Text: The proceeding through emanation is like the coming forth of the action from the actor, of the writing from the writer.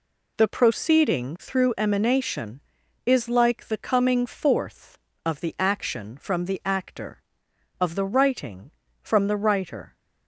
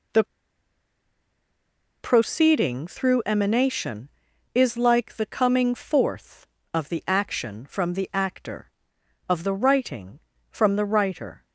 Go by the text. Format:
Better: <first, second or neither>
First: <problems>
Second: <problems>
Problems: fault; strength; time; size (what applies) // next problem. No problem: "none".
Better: first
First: none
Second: pauses between "The" and "proceeding"; strong; at 0.2 s; 1.7 s long